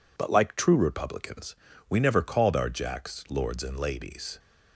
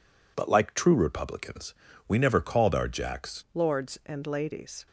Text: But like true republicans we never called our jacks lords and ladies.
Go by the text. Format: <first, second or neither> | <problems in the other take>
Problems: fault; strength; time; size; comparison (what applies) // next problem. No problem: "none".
first | pauses between "republicans" and "we"; slight; at 1.7 s; 0.34 s long; slight in the first // changes voice at "lords"; from 3.5 s on; 1.3 s long